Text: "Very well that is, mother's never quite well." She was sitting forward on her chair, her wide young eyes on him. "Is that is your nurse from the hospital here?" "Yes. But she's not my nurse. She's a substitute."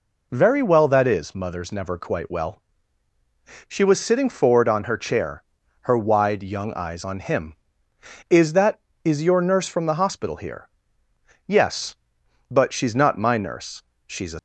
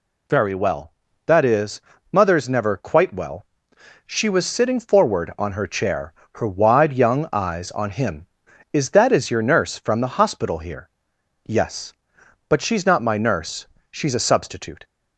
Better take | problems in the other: second | stops before "substitute"; at 14.3 s

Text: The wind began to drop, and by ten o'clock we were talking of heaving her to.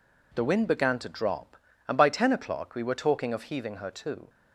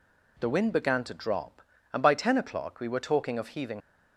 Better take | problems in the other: first | stops before "her to"; at 3.8 s

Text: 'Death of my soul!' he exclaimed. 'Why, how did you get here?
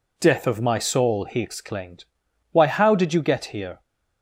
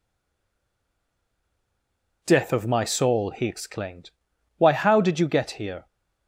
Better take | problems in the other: first | stays silent before the first word; until 2.2 s; 2.2 s long

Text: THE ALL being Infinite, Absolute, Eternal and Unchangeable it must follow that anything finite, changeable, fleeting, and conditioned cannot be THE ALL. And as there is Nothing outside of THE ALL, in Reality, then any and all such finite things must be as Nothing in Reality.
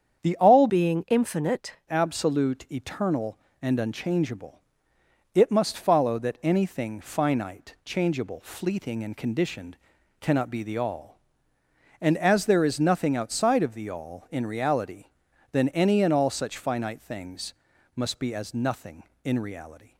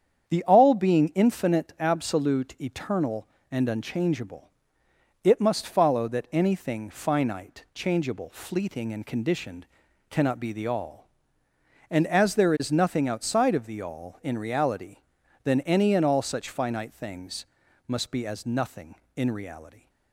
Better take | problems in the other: second | starts louder than the rest; strong; until 1.2 s; 8 dB; strong in the second // changes voice from "being" to "Infinite"; from 0.6 to 1.7 s; 1.1 s long // pauses between "Unchangeable" and "it"; noticeable; at 4.6 s; 0.72 s long; noticeable in the second // pauses between "conditioned" and "cannot"; at 9.7 s; 0.42 s long; also in the second // pauses between "things" and "must"; at 17.5 s; 0.42 s long; also in the second

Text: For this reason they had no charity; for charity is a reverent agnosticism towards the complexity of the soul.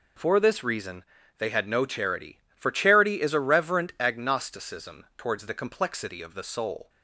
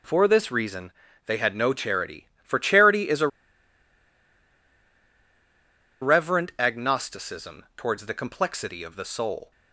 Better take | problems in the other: first | pauses between "reason" and "they"; slight; at 0.9 s; 0.34 s long; slight in the first // pauses between "a" and "reverent"; strong; at 3.2 s; 2.7 s long

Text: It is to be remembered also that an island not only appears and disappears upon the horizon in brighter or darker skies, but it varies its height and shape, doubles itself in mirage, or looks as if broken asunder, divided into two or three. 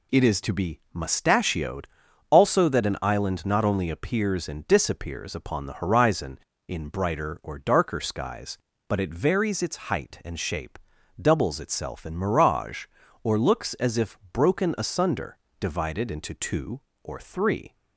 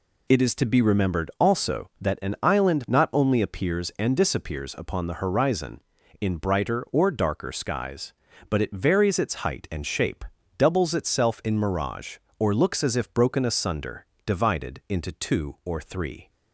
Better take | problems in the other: second | says "mustachioed" for "remembered"; at 0.9 s

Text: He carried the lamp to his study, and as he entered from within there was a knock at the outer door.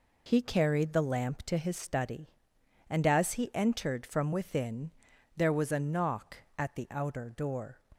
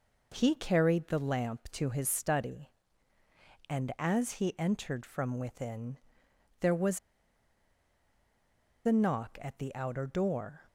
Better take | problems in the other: first | pauses between "within" and "there"; noticeable; at 5.9 s; 0.62 s long; noticeable in the first // pauses between "was" and "a"; strong; at 6.9 s; 1.8 s long

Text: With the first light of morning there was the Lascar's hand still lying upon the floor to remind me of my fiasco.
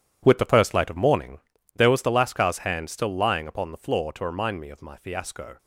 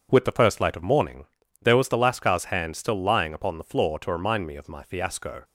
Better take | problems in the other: second | gets quieter; strong; throughout; 12.5 dB // pauses between "morning" and "there"; slight; at 1.3 s; 0.36 s long; slight in the second

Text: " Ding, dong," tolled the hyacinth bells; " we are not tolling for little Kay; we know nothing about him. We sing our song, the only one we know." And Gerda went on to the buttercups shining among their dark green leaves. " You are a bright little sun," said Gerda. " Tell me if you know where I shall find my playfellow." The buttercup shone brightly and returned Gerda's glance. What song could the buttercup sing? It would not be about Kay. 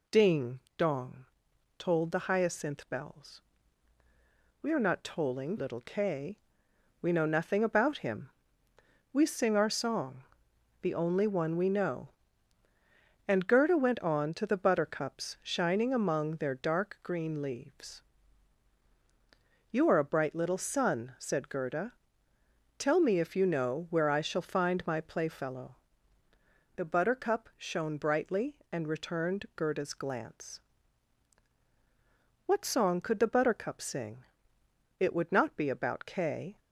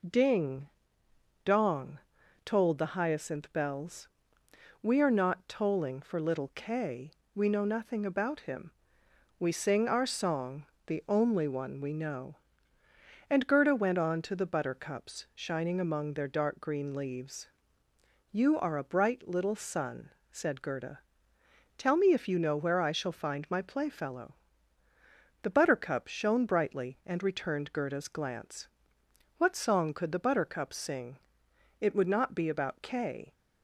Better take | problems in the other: second | skips "for"; at 5.5 s

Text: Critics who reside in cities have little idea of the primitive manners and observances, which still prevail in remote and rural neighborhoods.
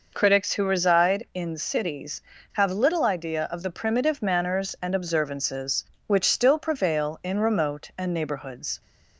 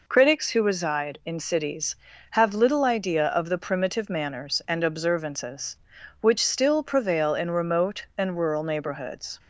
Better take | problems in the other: second | skips "rural"; at 8.1 s

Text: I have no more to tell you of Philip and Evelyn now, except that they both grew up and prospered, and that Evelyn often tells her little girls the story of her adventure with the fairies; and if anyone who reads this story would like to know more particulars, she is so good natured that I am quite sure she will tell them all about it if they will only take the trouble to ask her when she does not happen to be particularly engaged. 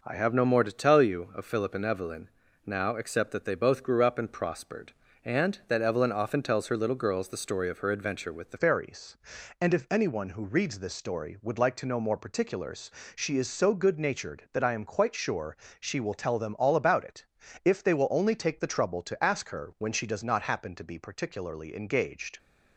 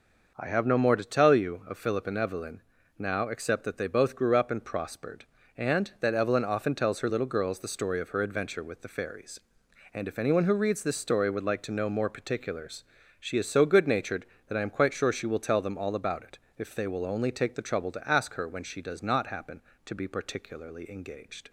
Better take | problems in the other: second | pauses between "Evelyn" and "now"; slight; at 2.2 s; 0.36 s long; slight in the second // changes voice at "fairies"; from 8.5 s on; 13.8 s long // pauses between "sure" and "she"; slight; at 15.5 s; 0.22 s long // pauses between "it" and "if"; at 17.2 s; 0.40 s long; slight in the second

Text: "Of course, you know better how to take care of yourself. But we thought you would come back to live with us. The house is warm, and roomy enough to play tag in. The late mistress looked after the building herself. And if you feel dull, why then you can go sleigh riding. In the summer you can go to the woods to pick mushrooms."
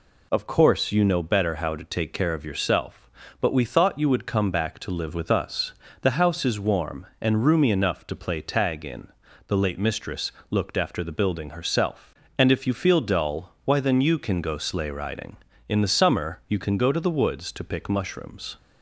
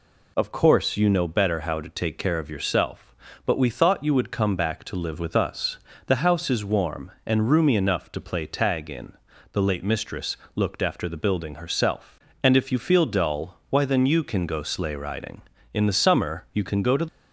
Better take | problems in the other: first | pauses between "mistress" and "looked"; slight; at 10.3 s; 0.20 s long; slight in the first // stops before "the woods to pick mushrooms"; at 17.0 s

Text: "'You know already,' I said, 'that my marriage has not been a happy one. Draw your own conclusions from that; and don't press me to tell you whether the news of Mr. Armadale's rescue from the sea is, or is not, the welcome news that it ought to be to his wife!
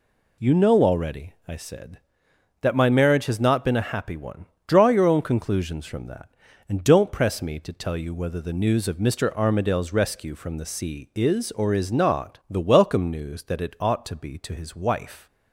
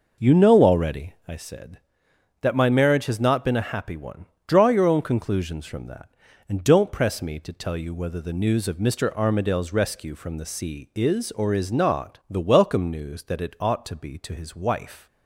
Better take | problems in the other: first | starts louder than the rest; noticeable; until 1.3 s; 5.5 dB

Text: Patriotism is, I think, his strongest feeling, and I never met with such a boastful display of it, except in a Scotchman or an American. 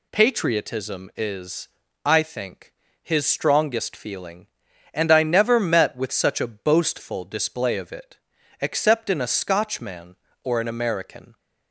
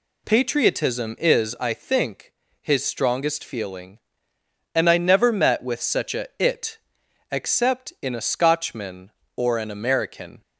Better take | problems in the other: first | skips "boastful display of"; at 6.3 s

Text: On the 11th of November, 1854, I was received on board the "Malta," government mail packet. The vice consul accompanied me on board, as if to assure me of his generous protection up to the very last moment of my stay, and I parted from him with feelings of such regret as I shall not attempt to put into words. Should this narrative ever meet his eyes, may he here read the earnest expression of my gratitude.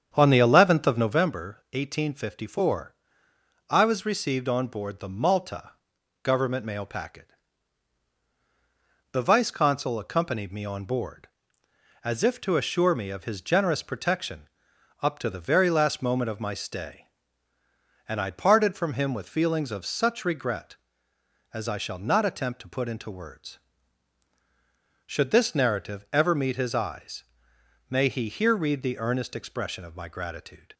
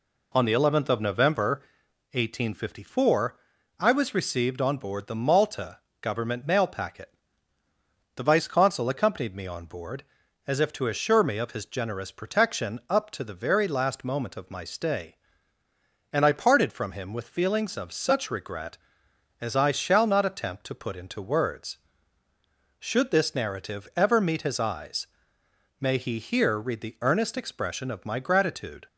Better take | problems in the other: second | starts louder than the rest; strong; until 1.3 s; 8 dB // pauses between "protection" and "up"; noticeable; at 14.4 s; 0.52 s long

